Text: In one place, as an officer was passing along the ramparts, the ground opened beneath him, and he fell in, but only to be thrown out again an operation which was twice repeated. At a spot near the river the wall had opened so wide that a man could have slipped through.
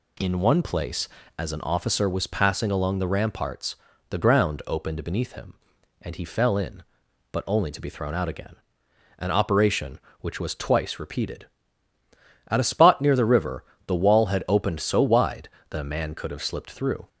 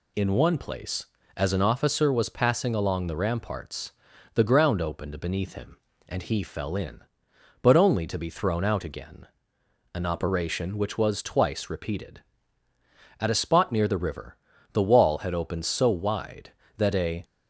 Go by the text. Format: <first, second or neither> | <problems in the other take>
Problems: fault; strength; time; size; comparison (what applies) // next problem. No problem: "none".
first | pauses between "again" and "an"; noticeable; at 9.2 s; 0.70 s long; noticeable in the first // pauses between "river" and "the"; slight; at 14.3 s; 0.36 s long; slight in the first // stops before "man could have slipped through"; at 17.2 s